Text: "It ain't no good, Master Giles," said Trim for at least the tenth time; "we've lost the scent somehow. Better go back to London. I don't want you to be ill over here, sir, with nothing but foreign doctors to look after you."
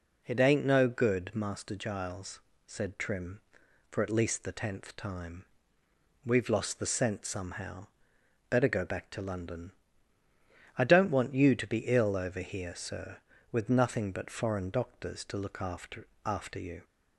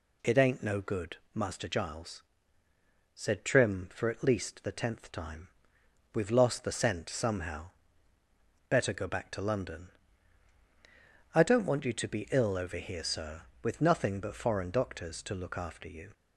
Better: second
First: says "after" twice; at 16.2 s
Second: none

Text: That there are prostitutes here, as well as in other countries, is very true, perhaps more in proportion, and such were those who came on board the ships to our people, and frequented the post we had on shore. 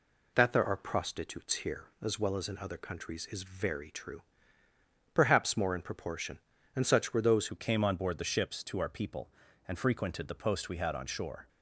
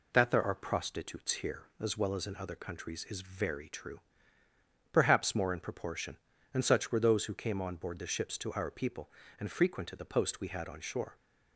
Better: second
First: changes voice at "who"; from 7.4 s on; 4.0 s long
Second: none

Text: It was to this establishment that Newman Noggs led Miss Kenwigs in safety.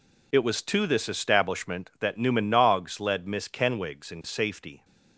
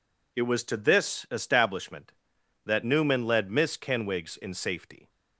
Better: first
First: none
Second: skips "Noggs"; at 3.2 s

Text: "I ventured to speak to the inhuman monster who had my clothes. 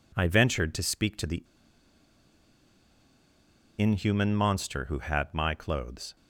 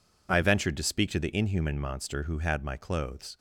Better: second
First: pauses between "the" and "inhuman"; strong; at 1.4 s; 2.3 s long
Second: none

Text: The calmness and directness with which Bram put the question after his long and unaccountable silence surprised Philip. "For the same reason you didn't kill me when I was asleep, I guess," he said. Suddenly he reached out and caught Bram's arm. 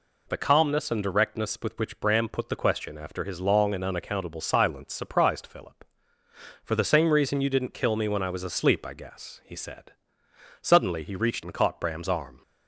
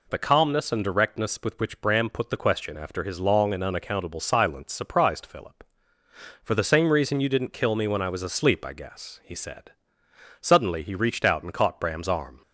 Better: second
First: skips "out"; at 11.4 s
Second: none

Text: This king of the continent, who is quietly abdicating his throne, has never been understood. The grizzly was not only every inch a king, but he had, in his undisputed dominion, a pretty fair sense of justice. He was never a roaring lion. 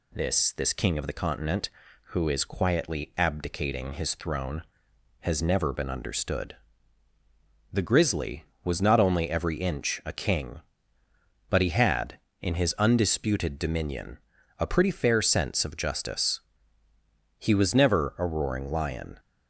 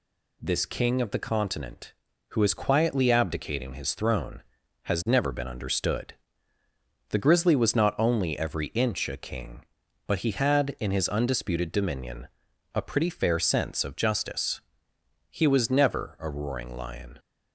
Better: second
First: says "This" twice; at 0.5 s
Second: none

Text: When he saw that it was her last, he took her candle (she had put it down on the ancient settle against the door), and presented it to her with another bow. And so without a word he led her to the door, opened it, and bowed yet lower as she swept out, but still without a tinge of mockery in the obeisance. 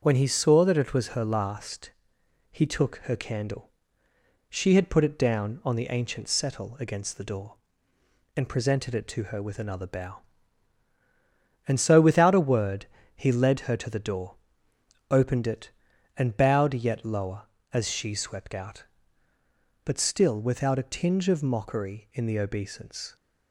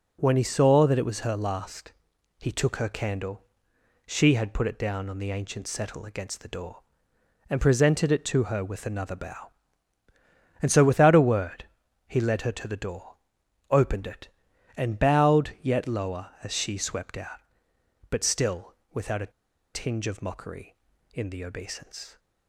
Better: first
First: pauses between "word" and "he"; slight; at 12.8 s; 0.28 s long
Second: pauses between "word" and "he"; at 11.6 s; 0.42 s long // pauses between "still" and "without"; slight; at 18.7 s; 0.18 s long // pauses between "a" and "tinge"; at 19.3 s; 0.42 s long

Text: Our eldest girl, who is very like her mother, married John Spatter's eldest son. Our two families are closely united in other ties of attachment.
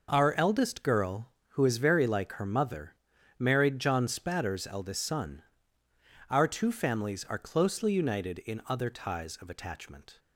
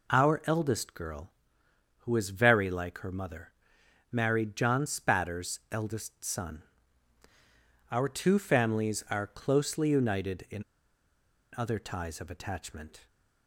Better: first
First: none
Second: pauses between "in" and "other"; noticeable; at 10.6 s; 0.93 s long

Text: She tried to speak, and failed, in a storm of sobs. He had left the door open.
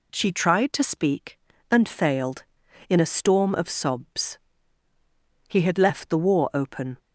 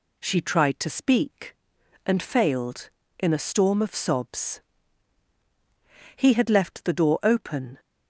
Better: second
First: says "war" for "door"; at 6.1 s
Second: none

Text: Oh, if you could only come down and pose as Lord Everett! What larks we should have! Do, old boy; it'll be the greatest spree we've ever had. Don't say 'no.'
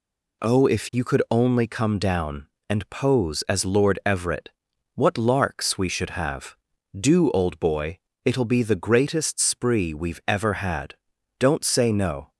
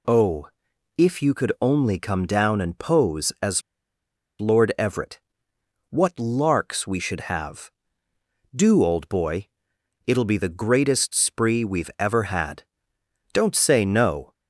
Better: first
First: none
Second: pauses between "as" and "Lord"; noticeable; at 3.6 s; 0.79 s long

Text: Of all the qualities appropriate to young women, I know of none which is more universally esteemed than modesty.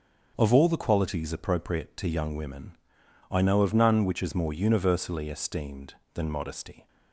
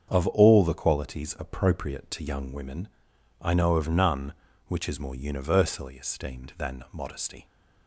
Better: neither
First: starts louder than the rest; until 1.3 s; 6.5 dB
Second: starts louder than the rest; strong; until 1.1 s; 7.5 dB

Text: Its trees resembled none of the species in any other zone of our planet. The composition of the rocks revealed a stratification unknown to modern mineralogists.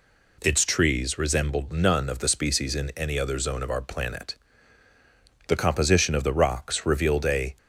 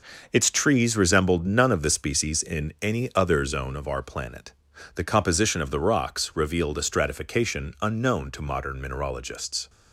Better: second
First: stops before "stratification unknown to modern mineralogists"; at 7.5 s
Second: none

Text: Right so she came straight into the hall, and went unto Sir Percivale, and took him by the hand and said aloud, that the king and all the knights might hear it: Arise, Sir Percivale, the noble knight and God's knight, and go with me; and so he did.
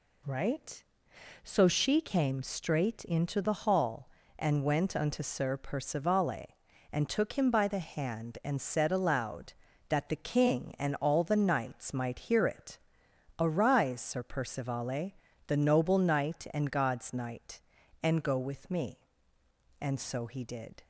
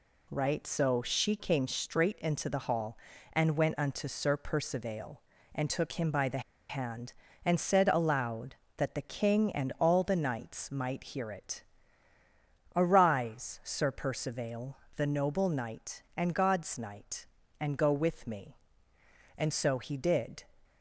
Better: first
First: none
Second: pauses between "the" and "hand"; slight; at 6.3 s; 0.29 s long

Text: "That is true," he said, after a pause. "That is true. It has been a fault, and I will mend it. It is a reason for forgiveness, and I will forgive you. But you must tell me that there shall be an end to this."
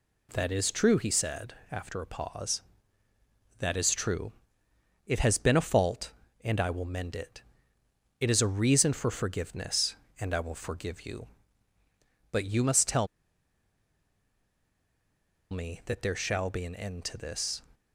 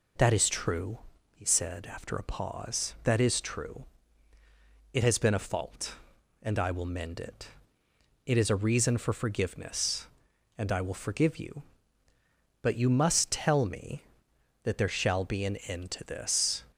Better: second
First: pauses between "tell" and "me"; strong; at 13.0 s; 2.4 s long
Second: none

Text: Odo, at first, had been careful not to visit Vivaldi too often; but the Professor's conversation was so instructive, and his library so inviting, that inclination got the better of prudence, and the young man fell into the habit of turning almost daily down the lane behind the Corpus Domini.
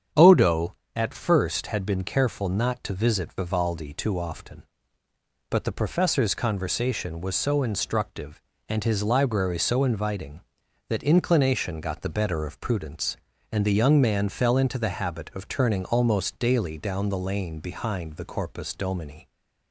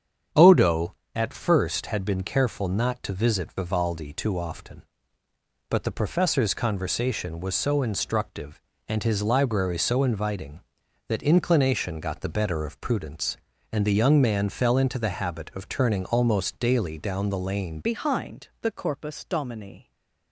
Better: first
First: starts louder than the rest; strong; until 1.3 s; 8 dB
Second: starts louder than the rest; strong; until 1.5 s; 8 dB // changes voice at "behind"; from 17.8 s on; 2.1 s long // stays silent after the last word; slight; from 19.8 s on; 0.5 s long

